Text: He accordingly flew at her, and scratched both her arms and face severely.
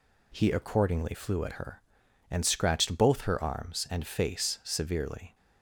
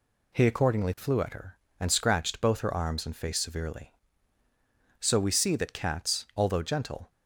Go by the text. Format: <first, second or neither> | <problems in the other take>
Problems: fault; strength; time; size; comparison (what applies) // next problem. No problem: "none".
first | goes on to say "So we see that cats although gentle"; strong; from 5.0 s on; 2.1 s long